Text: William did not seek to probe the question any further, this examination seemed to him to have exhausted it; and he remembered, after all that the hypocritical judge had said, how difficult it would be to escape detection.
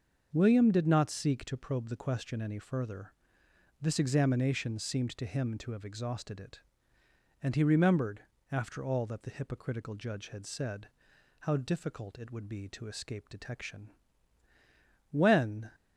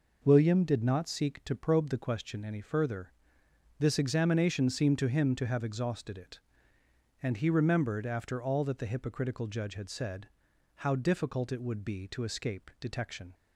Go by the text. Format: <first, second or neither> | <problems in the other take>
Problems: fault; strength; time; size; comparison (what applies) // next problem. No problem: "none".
second | starts louder than the rest; until 1.3 s; 6.5 dB // goes on to say "When"; from 15.1 s on; 0.58 s long